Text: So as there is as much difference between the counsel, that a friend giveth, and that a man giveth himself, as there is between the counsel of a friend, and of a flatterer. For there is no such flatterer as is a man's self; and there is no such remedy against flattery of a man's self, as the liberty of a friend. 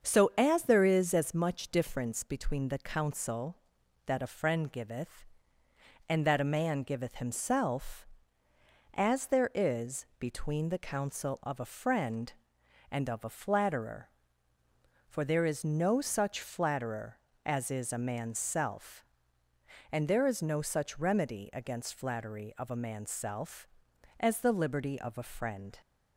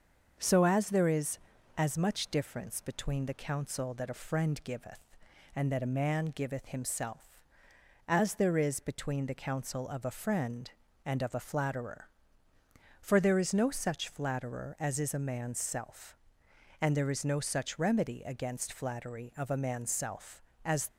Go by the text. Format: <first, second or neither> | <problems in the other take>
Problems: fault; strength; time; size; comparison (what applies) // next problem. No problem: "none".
first | starts louder than the rest; until 1.3 s; 6.5 dB; also in the first // stops before "the liberty of a friend"; at 20.8 s